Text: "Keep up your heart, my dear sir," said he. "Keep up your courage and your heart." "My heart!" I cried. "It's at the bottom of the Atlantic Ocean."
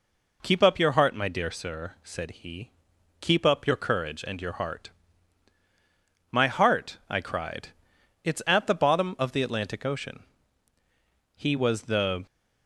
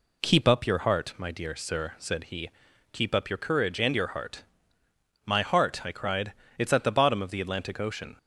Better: second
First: goes on to say "He was the"; noticeable; from 11.3 s on; 0.90 s long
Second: none

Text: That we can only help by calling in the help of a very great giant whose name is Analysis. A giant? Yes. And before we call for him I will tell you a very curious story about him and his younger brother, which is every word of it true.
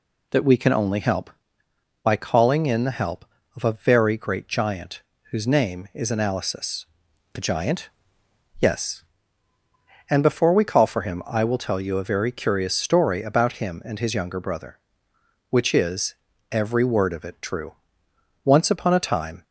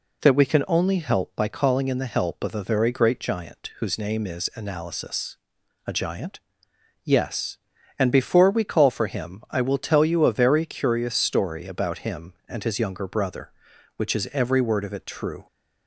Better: second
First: pauses between "giant" and "whose"; slight; at 5.0 s; 0.30 s long // pauses between "is" and "every"; slight; at 16.1 s; 0.36 s long // goes on to say "Once upon a time"; noticeable; from 18.4 s on; 1.0 s long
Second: none

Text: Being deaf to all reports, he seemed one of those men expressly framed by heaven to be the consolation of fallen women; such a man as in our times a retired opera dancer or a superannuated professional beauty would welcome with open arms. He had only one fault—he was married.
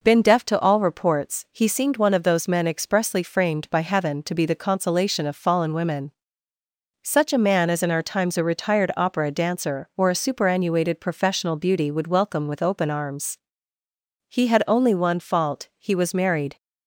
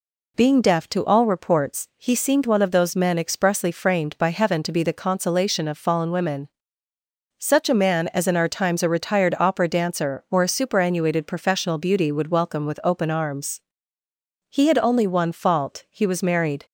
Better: second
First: says "Been" for "Being"; at 0.0 s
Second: none

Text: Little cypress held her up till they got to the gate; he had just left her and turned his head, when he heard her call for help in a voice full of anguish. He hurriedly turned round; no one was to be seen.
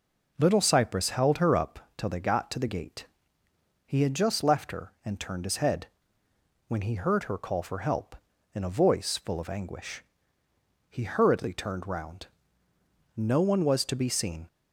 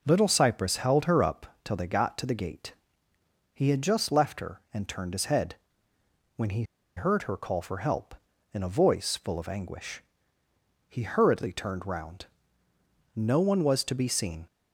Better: first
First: none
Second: pauses between "he" and "heard"; slight; at 6.6 s; 0.33 s long

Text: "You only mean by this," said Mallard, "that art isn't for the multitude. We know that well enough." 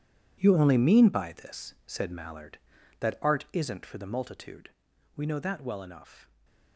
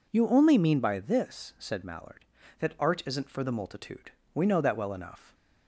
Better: second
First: gets quieter; strong; throughout; 13.5 dB // stays silent after the last word; slight; from 6.2 s on; 0.5 s long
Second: none

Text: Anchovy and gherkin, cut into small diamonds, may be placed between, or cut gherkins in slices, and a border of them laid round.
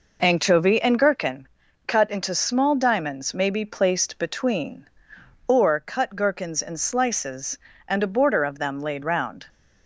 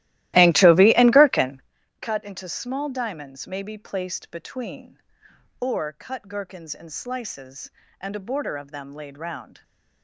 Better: first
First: none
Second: starts louder than the rest; strong; until 1.7 s; 16 dB

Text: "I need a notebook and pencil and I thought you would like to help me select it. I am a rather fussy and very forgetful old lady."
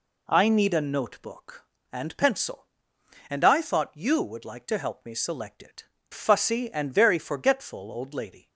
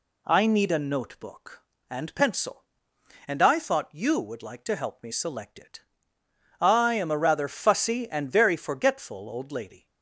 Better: second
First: skips "I am a rather"; at 5.9 s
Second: none

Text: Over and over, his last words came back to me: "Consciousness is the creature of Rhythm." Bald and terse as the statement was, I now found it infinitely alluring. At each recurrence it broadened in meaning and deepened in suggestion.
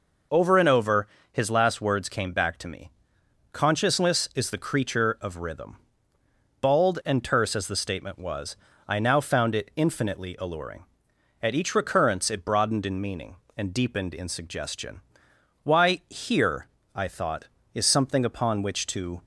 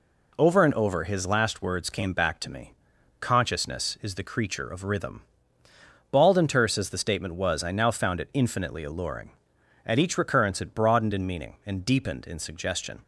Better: second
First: goes on to say "Why here I thought is something upon which to"; strong; from 15.6 s on; 3.6 s long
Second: none

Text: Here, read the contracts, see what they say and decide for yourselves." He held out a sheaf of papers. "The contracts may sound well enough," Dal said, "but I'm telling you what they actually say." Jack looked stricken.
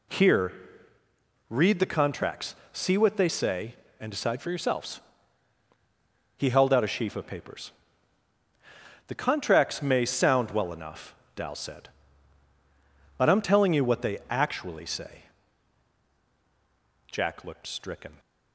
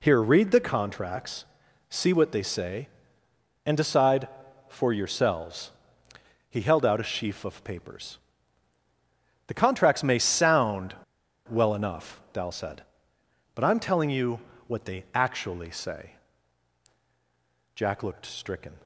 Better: first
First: none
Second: pauses between "sound" and "well"; noticeable; at 10.9 s; 0.53 s long // pauses between "you" and "what"; slight; at 14.3 s; 0.28 s long

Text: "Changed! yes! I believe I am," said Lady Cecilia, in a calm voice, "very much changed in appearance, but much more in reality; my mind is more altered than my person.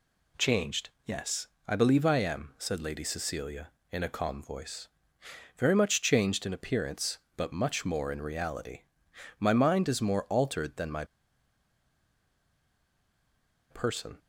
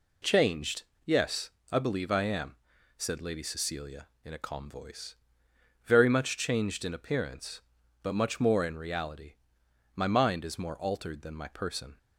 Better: second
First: pauses between "my" and "person"; strong; at 11.0 s; 2.6 s long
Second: none

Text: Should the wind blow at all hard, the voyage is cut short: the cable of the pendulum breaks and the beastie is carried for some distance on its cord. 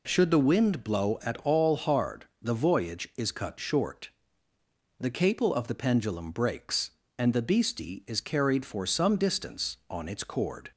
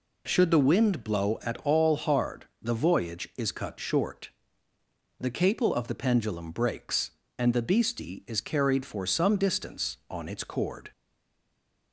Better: first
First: none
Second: stays silent after the last word; from 10.9 s on; 1.0 s long

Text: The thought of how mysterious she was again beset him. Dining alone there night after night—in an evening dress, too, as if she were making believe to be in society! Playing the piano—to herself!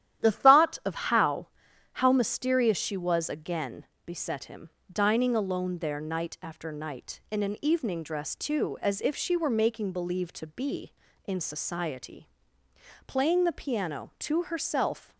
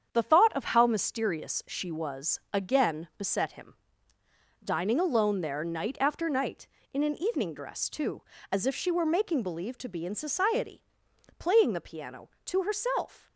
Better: second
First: starts louder than the rest; strong; until 1.2 s; 11.5 dB // says "how" twice; at 1.9 s // pauses between "again" and "beset"; slight; at 3.8 s; 0.20 s long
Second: starts louder than the rest; strong; until 1.1 s; 8 dB

